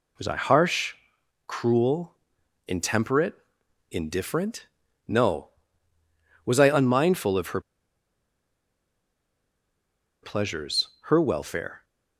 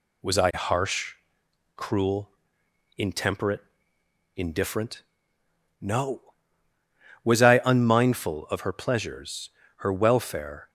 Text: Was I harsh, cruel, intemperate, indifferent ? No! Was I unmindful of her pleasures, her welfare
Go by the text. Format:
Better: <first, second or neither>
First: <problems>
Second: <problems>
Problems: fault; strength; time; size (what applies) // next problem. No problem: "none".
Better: second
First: pauses between "her" and "pleasures"; strong; at 7.5 s; 2.6 s long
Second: none